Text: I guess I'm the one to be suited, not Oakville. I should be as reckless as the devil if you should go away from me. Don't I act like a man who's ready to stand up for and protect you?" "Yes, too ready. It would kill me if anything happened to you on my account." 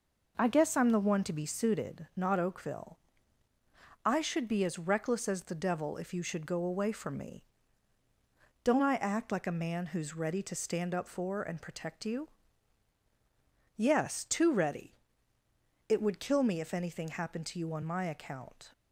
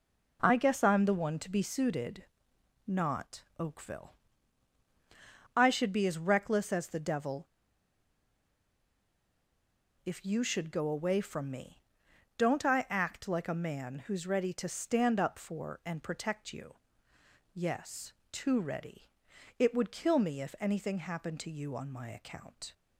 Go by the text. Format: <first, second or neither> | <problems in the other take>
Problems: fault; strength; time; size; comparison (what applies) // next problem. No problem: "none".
first | pauses between "not" and "Oakville"; slight; at 3.4 s; 0.16 s long // pauses between "devil" and "if"; strong; at 7.4 s; 2.5 s long